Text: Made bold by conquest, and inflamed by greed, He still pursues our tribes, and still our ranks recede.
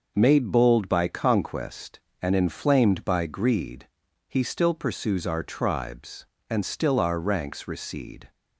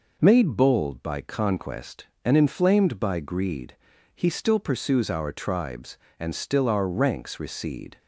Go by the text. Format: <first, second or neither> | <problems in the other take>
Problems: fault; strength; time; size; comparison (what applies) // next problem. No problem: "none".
neither | none